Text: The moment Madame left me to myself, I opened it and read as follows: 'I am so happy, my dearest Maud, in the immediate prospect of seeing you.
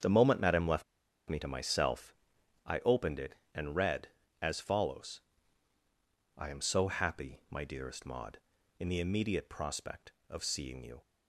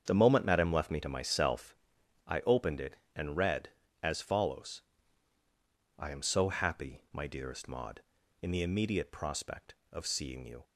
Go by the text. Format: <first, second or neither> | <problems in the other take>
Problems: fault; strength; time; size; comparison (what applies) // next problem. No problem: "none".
second | starts louder than the rest; strong; until 1.4 s; 7.5 dB; strong in the second // pauses between "left" and "me"; at 0.8 s; 0.43 s long